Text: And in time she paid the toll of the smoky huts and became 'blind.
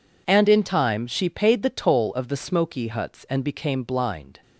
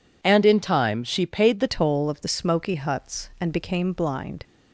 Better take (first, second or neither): first